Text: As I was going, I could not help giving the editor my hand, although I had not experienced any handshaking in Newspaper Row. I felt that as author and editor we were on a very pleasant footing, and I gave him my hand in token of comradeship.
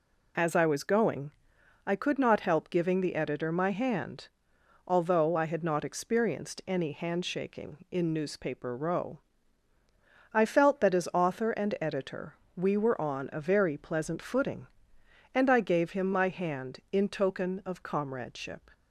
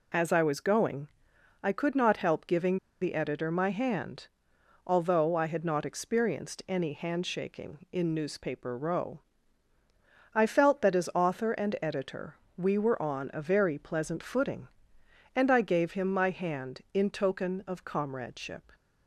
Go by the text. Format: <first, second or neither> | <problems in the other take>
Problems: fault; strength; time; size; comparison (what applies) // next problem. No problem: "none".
first | pauses between "giving" and "the"; slight; at 2.7 s; 0.24 s long // pauses between "editor" and "we"; slight; at 12.3 s; 0.22 s long; slight in the first